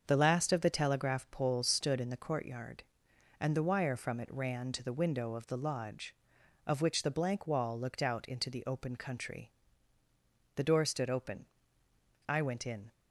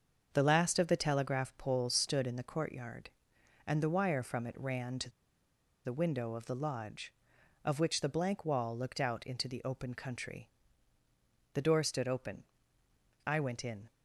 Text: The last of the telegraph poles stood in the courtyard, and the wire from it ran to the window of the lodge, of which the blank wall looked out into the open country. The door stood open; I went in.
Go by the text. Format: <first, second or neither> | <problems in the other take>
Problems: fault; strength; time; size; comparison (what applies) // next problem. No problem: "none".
first | starts louder than the rest; until 1.3 s; 6.5 dB; also in the first // pauses between "to" and "the"; noticeable; at 5.0 s; 0.76 s long